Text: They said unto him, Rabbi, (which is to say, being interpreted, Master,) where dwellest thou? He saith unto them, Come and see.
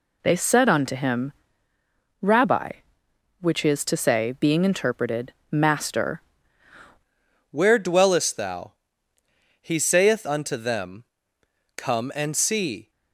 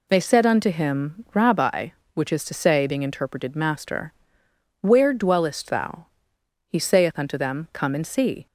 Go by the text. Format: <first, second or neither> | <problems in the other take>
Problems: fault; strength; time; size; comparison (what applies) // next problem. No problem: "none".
second | changes voice at "where"; from 7.5 s on; 5.4 s long